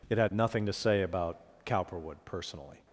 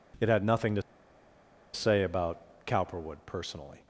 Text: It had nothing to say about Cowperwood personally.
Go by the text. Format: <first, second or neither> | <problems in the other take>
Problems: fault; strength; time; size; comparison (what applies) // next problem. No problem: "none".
first | pauses between "to" and "say"; noticeable; at 0.8 s; 0.92 s long